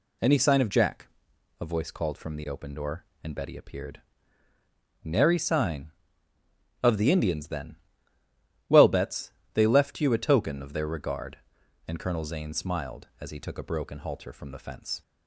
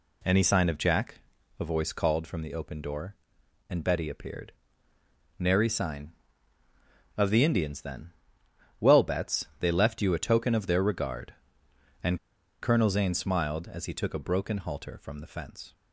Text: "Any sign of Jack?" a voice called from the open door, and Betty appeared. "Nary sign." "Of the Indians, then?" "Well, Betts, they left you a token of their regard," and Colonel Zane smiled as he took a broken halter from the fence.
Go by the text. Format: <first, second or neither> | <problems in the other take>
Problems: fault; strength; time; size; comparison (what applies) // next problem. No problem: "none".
first | pauses between "and" and "Colonel"; at 12.1 s; 0.45 s long